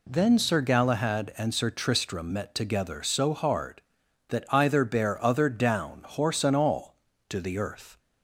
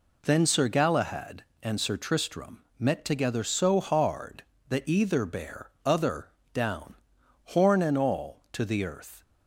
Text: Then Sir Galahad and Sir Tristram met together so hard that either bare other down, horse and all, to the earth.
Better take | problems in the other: first | pauses between "Tristram" and "met"; slight; at 2.6 s; 0.16 s long // pauses between "other" and "down"; slight; at 6.2 s; 0.24 s long // says "horn" for "horse"; at 7.4 s

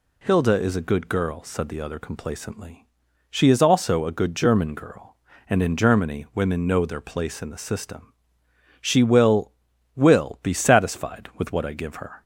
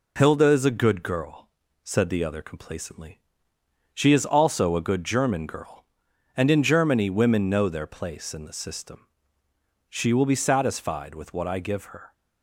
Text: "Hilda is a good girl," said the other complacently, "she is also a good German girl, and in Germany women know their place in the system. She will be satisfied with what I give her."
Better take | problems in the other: second | says "will" twice; at 9.9 s

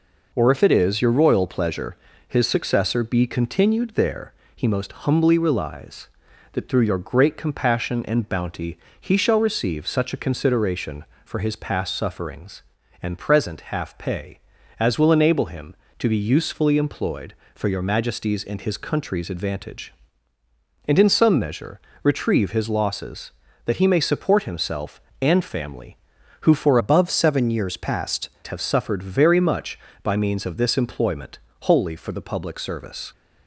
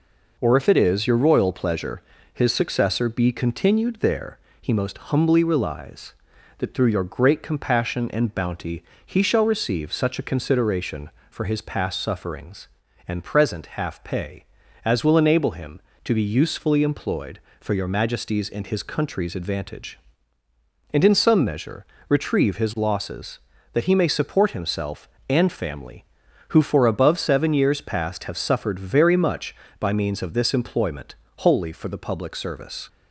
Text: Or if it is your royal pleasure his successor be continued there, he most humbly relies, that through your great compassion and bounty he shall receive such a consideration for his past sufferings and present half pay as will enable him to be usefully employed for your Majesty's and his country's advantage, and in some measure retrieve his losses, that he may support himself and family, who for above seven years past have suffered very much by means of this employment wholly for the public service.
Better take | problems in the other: second | pauses between "pleasure" and "his"; slight; at 1.9 s; 0.32 s long; slight in the second // pauses between "bounty" and "he"; slight; at 8.7 s; 0.22 s long; slight in the second // pauses between "measure" and "retrieve"; slight; at 21.8 s; 0.22 s long; slight in the second // changes voice from "above" to "past"; from 26.7 to 28.2 s; 1.5 s long // pauses between "employment" and "wholly"; slight; at 31.3 s; 0.26 s long; slight in the second

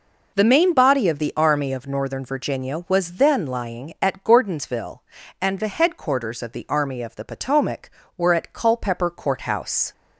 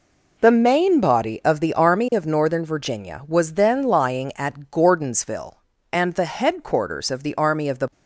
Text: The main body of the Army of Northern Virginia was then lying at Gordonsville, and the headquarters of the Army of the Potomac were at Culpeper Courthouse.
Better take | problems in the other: first | stops before "Potomac were at Culpeper Courthouse"; at 7.9 s

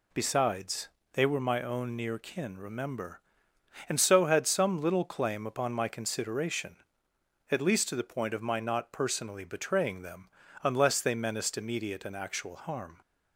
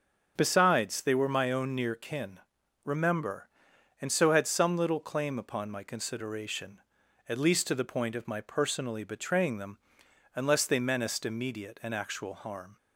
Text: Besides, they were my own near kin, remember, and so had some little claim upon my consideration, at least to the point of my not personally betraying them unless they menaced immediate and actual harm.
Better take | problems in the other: first | starts louder than the rest; until 1.3 s; 6.5 dB // skips "not"; at 8.4 s // pauses between "them" and "unless"; noticeable; at 9.7 s; 0.56 s long; slight in the first

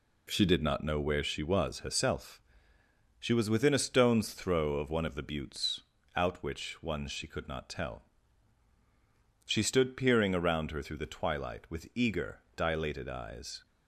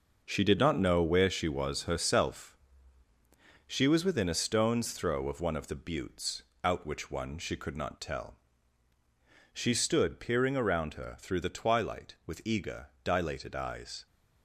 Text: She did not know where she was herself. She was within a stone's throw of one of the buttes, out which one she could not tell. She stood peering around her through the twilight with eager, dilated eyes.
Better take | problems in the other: first | gets quieter; strong; throughout; 8.5 dB

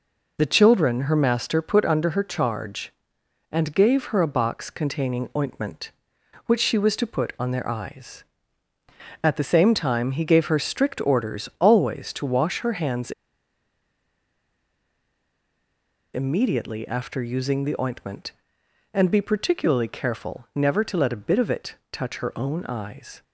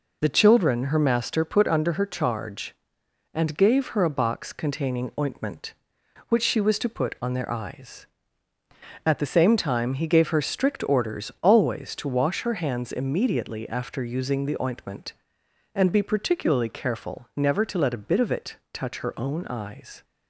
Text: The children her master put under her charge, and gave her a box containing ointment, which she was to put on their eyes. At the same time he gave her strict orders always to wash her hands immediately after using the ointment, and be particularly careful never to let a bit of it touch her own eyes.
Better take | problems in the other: second | pauses between "hands" and "immediately"; strong; at 13.1 s; 3.0 s long // pauses between "it" and "touch"; slight; at 21.7 s; 0.18 s long; slight in the second

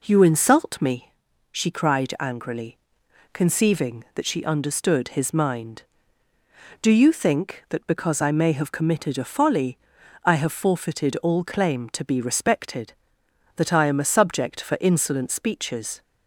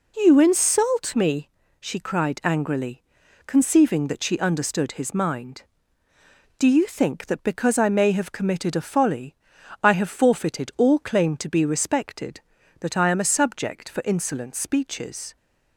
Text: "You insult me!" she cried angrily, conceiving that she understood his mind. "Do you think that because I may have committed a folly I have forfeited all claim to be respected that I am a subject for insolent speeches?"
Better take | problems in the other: neither | pauses between "folly" and "I"; noticeable; the same in both

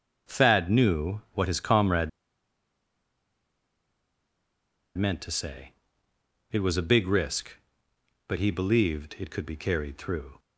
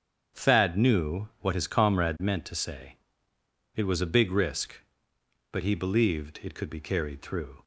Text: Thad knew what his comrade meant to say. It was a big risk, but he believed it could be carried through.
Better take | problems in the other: second | starts louder than the rest; strong; until 1.4 s; 7.5 dB; strong in the second // pauses between "comrade" and "meant"; strong; at 2.0 s; 2.8 s long

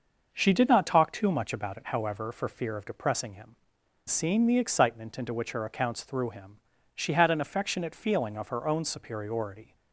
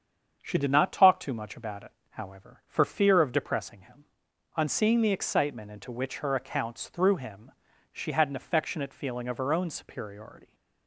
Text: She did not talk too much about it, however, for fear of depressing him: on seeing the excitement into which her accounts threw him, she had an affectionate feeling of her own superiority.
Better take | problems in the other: second | starts louder than the rest; noticeable; until 1.3 s; 6 dB; strong in the second // skips "on"; at 3.8 s

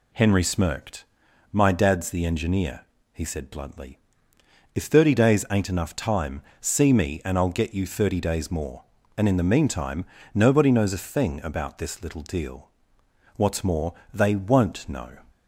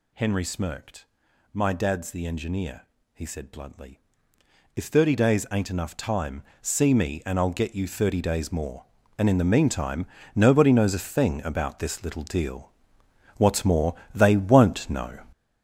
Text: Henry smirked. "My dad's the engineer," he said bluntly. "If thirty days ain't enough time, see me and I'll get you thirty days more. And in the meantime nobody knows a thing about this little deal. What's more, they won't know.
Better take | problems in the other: first | gets louder; strong; throughout; 8 dB // pauses between "meantime" and "nobody"; slight; at 10.0 s; 0.30 s long; slight in the first

